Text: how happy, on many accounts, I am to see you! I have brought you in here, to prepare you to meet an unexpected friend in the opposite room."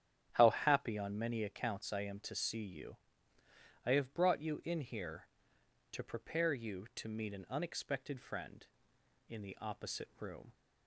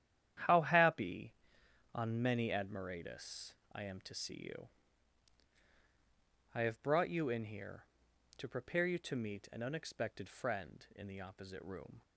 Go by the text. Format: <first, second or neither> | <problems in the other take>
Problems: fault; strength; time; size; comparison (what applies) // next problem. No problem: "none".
first | starts louder than the rest; strong; until 2.0 s; 10.5 dB; strong in the first // says "admiratus" for "accounts"; at 2.5 s